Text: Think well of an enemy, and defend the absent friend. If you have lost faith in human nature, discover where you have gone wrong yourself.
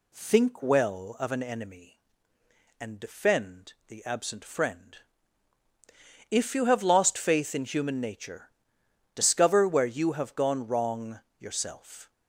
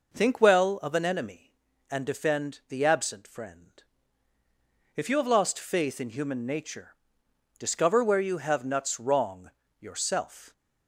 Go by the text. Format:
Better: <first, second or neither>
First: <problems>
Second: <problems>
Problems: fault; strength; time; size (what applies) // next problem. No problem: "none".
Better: first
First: pauses between "wrong" and "yourself"; slight; at 11.2 s; 0.18 s long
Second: says "nuts" for "gone"; at 8.6 s // pauses between "wrong" and "yourself"; slight; at 9.4 s; 0.32 s long